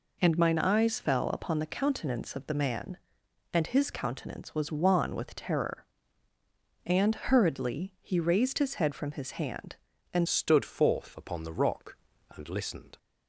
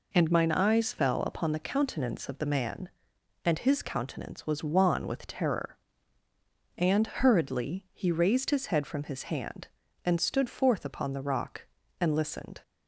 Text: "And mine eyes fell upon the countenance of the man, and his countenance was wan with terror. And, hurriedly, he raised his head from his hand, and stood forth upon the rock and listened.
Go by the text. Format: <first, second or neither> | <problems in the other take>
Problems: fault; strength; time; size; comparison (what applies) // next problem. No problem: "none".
second | changes voice at "stood"; from 10.2 s on; 2.7 s long